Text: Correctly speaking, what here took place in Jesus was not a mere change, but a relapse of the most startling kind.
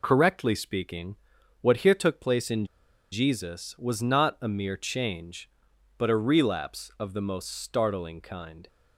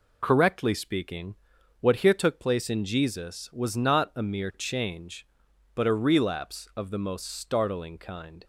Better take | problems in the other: second | pauses between "in" and "Jesus"; at 2.6 s; 0.45 s long

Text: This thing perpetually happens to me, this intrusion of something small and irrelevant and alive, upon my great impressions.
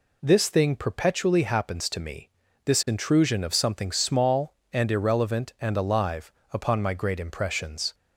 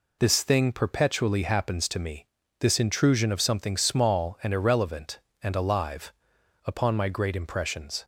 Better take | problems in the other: neither | none

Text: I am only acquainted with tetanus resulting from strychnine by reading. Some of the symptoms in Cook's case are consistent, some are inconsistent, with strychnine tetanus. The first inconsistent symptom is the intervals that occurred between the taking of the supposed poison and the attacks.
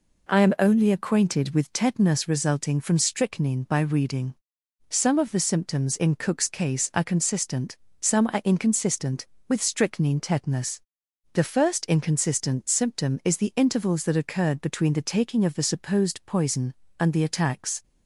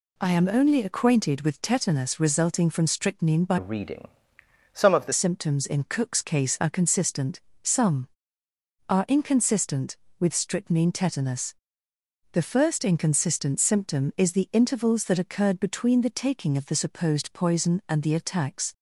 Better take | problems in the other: first | changes voice from "reading" to "the"; from 3.5 to 5.1 s; 1.6 s long

